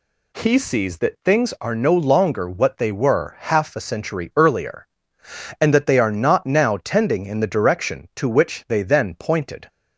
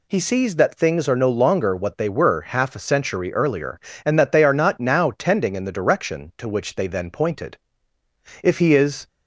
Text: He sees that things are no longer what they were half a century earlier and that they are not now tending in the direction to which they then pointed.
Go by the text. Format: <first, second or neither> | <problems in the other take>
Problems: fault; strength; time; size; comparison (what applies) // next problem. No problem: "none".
first | goes on to say "If he is"; noticeable; from 8.4 s on; 0.66 s long